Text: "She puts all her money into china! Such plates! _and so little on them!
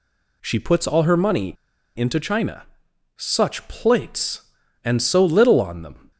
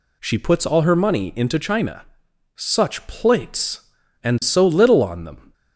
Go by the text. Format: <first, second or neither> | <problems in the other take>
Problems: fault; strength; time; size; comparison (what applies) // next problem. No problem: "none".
second | pauses between "money" and "into"; at 1.5 s; 0.42 s long